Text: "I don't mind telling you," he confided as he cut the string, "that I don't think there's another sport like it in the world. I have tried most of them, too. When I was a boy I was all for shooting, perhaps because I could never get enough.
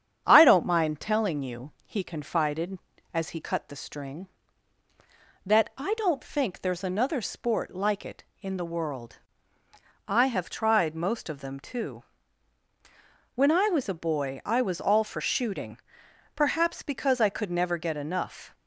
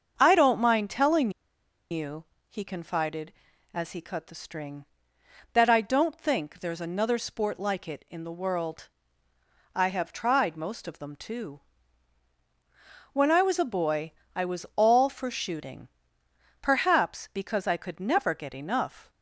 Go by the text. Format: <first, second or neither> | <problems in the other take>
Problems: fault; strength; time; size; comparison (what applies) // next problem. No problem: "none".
first | starts louder than the rest; until 1.1 s; 6.5 dB; strong in the first // pauses between "telling" and "you"; noticeable; at 1.3 s; 0.59 s long // pauses between "boy" and "I"; slight; at 14.1 s; 0.24 s long